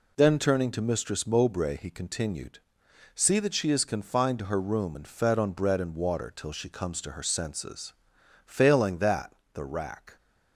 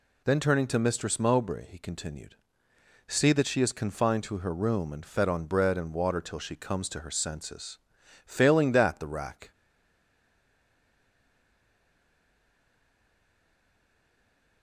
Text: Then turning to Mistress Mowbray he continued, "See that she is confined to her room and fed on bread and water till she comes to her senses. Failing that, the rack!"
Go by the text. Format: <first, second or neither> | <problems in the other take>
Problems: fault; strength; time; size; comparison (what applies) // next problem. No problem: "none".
first | stays silent after the last word; strong; from 9.5 s on; 5.1 s long